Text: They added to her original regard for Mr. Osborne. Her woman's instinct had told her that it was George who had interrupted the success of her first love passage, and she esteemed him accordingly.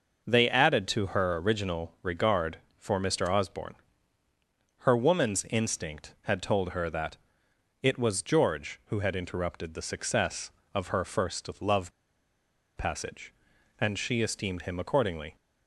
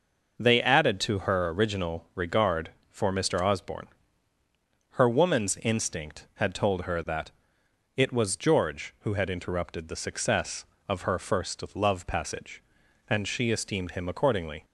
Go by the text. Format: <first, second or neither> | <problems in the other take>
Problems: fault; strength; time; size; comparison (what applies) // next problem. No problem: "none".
second | pauses between "that" and "it"; noticeable; at 7.1 s; 0.64 s long; noticeable in the second // pauses between "love" and "passage"; noticeable; at 11.9 s; 0.86 s long